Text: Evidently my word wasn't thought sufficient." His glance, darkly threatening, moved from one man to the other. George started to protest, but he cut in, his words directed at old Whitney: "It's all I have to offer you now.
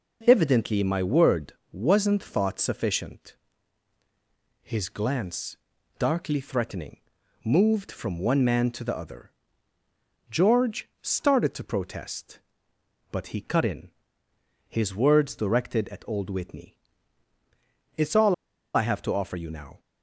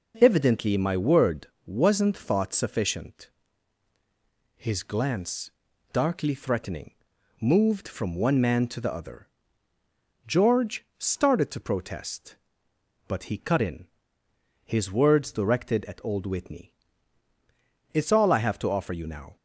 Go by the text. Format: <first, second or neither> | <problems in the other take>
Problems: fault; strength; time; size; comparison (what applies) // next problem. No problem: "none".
second | pauses between "word" and "wasn't"; slight; at 1.5 s; 0.18 s long; slight in the second // pauses between "all" and "I"; at 18.3 s; 0.41 s long